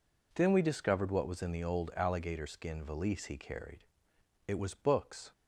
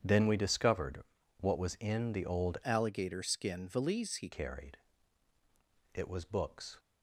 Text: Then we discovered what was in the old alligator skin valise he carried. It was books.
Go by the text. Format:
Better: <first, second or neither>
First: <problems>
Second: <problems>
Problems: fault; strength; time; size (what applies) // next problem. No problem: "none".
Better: first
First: none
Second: starts louder than the rest; strong; until 1.0 s; 8.5 dB // pauses between "discovered" and "what"; at 1.0 s; 0.38 s long // changes voice from "alligator" to "he"; from 2.6 to 4.2 s; 1.6 s long